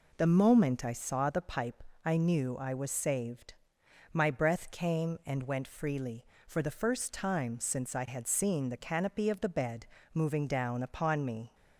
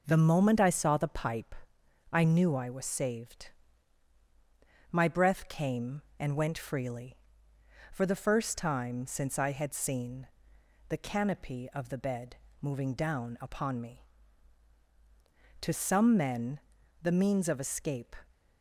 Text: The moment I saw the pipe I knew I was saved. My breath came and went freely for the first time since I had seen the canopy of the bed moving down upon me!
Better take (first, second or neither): first